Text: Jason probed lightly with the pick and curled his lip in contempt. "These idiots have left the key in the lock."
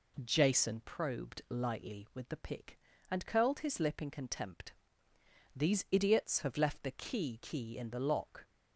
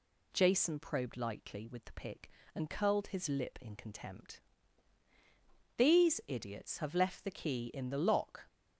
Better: second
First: says "key" twice; at 7.4 s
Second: none

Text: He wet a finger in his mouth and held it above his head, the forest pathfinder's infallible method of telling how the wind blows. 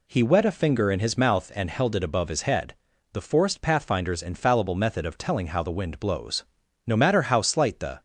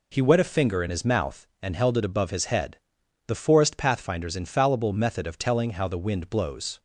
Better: second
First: goes on to say "No matter how slight the"; noticeable; from 6.8 s on; 1.1 s long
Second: none

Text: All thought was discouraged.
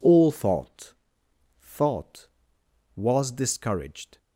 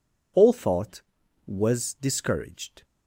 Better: second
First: says "thought" twice; at 1.6 s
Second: none

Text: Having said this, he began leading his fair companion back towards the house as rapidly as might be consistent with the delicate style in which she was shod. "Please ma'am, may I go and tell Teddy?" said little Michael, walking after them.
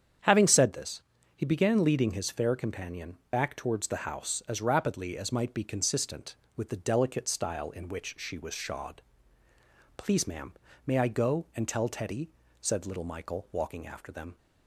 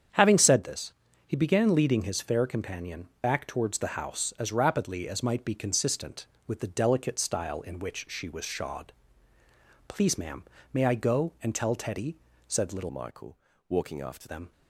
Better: first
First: starts louder than the rest; strong; until 1.5 s; 8 dB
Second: starts louder than the rest; strong; until 1.4 s; 8 dB // changes voice from "Michael" to "after"; from 12.9 to 14.2 s; 1.3 s long

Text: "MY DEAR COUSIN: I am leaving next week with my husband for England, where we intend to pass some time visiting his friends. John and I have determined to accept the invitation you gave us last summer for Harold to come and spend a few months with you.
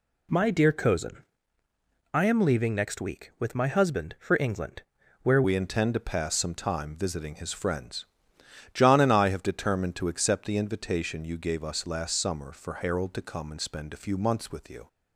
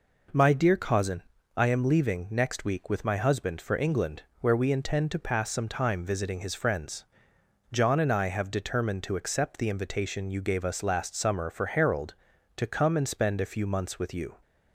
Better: second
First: changes voice at "we"; from 5.4 s on; 9.4 s long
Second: none

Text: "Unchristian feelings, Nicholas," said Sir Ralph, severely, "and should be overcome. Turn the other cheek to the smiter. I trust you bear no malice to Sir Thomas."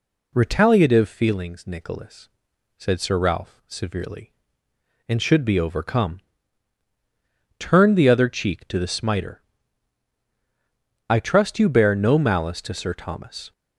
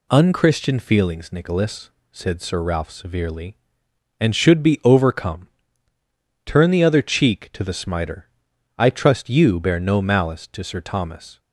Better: second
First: says "Retaliative" for "Unchristian"; at 0.3 s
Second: none

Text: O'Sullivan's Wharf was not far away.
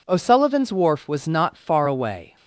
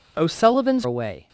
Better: first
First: none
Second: skips "Wharf was not far"; at 0.8 s

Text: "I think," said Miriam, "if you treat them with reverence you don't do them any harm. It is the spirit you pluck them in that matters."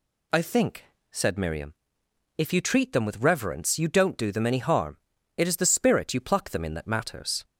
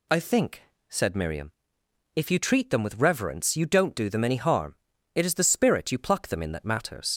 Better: first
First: none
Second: leaves "matters" unfinished; at 7.1 s; 60 ms

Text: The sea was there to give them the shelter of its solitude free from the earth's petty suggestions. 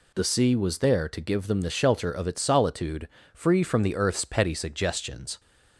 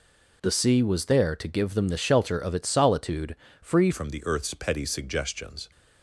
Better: first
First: pauses between "solitude" and "free"; slight; at 3.0 s; 0.24 s long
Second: pauses between "solitude" and "free"; slight; at 3.3 s; 0.24 s long // changes voice at "from"; from 3.9 s on; 1.8 s long

